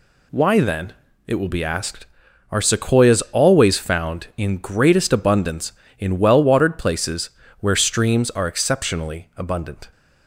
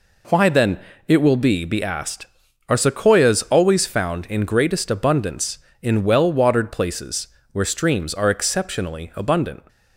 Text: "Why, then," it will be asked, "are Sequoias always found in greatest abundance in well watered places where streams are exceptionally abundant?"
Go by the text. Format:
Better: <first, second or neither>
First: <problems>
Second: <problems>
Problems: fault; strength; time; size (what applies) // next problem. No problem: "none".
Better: first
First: pauses between "places" and "where"; slight; at 7.3 s; 0.30 s long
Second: says "be" twice; at 1.6 s // pauses between "places" and "where"; slight; at 7.2 s; 0.24 s long